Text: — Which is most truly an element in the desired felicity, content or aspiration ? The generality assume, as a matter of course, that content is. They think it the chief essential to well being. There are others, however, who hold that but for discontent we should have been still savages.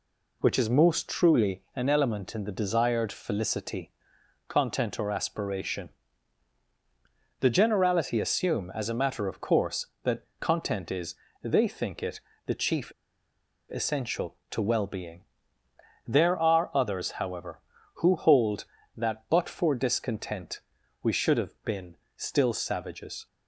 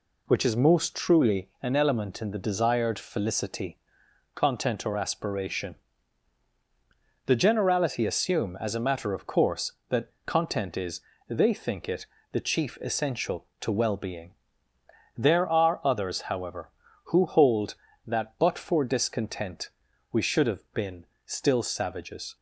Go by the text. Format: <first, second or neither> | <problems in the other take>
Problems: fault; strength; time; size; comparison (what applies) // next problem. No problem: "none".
second | pauses between "it" and "the"; slight; at 12.1 s; 0.28 s long; slight in the second // pauses between "chief" and "essential"; noticeable; at 12.9 s; 0.81 s long // pauses between "discontent" and "we"; at 20.6 s; 0.42 s long; also in the second // pauses between "been" and "still"; slight; at 21.9 s; 0.18 s long; slight in the second